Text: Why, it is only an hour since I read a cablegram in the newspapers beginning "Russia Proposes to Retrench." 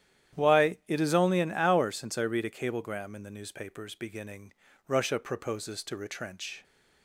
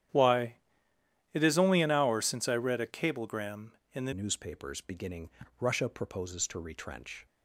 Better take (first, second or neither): first